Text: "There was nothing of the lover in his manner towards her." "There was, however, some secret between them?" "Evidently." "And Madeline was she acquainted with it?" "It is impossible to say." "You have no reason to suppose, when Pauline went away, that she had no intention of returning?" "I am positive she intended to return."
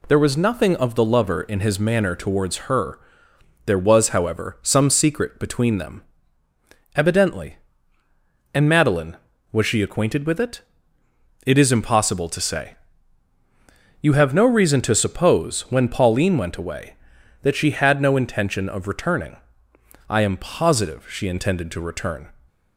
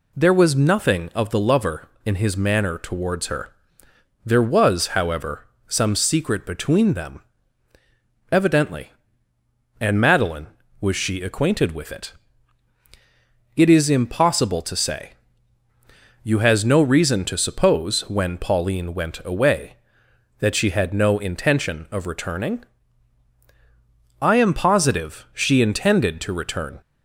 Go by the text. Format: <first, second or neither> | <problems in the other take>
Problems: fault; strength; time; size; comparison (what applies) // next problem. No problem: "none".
first | says "has" for "have"; at 16.3 s